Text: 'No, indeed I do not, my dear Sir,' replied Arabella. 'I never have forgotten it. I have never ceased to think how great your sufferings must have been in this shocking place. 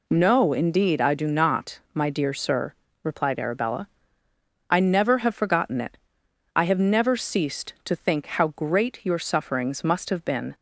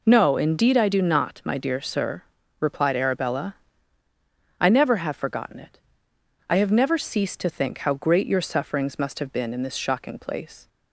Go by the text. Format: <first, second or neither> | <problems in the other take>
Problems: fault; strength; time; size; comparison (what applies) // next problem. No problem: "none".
second | stops before "in this shocking place"; at 10.5 s